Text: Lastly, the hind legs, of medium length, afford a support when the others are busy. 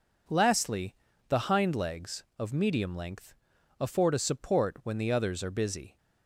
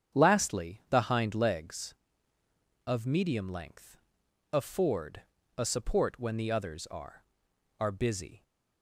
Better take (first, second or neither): first